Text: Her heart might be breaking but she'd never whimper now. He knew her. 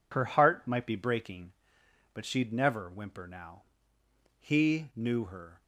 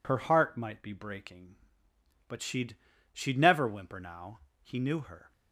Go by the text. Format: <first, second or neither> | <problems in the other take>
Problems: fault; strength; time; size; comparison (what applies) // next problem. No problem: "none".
first | says "she'd" twice; at 3.1 s